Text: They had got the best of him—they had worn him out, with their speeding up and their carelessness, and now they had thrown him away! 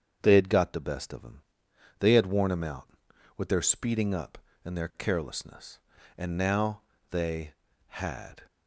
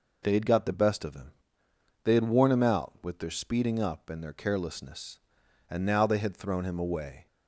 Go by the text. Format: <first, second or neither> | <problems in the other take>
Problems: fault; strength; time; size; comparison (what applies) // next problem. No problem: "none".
second | starts louder than the rest; strong; until 1.2 s; 7 dB // pauses between "now" and "they"; slight; at 6.8 s; 0.30 s long // stops before "thrown him away"; at 8.4 s